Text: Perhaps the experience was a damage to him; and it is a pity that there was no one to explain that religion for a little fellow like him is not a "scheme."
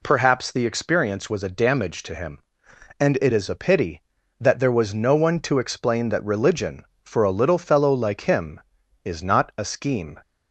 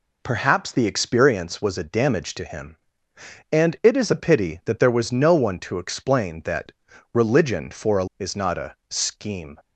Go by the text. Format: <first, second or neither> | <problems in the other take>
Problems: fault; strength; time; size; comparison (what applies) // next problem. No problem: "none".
first | pauses between "that" and "religion"; at 6.7 s; 0.40 s long // skips "little fellow like him"; at 8.1 s